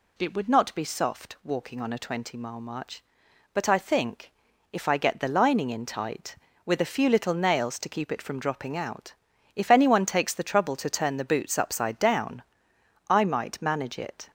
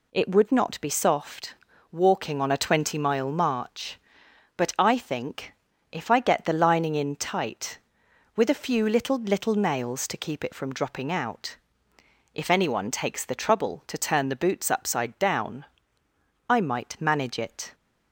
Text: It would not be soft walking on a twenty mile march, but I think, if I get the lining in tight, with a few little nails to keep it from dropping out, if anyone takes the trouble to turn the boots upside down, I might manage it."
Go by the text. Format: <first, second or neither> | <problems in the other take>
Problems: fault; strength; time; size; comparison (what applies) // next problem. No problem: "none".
first | pauses between "soft" and "walking"; slight; at 1.5 s; 0.36 s long // says "little" twice; at 9.1 s